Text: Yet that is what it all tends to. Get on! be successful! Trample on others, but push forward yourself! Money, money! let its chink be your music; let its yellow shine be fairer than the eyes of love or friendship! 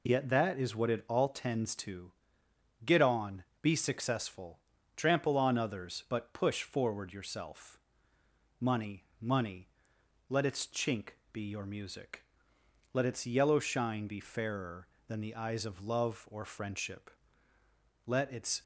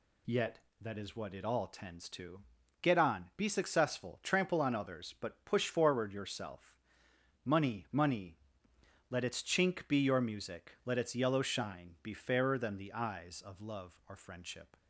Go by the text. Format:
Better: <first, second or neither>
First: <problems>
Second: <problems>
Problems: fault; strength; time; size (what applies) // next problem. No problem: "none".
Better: second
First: pauses between "chink" and "be"; slight; at 11.1 s; 0.15 s long // goes on to say "Let its"; from 18.0 s on; 0.56 s long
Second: none